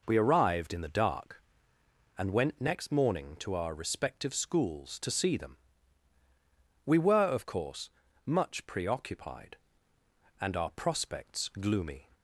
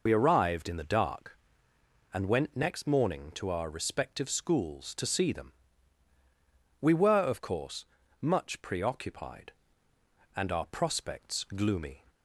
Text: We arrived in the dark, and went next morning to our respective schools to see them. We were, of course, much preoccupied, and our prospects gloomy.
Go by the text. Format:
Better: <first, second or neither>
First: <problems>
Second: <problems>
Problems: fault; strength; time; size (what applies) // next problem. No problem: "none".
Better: first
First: none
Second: loses the start of "We"; at 0.0 s; 55 ms